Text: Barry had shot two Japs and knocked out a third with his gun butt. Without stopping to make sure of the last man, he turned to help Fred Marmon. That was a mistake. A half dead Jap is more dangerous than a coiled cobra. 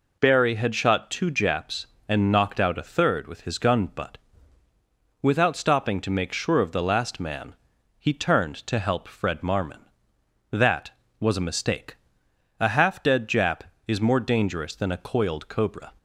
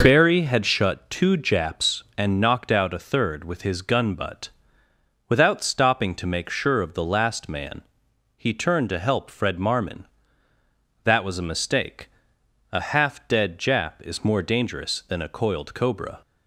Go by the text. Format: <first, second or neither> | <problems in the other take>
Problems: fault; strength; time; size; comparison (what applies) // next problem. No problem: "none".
first | says "shut" for "shot"; at 0.6 s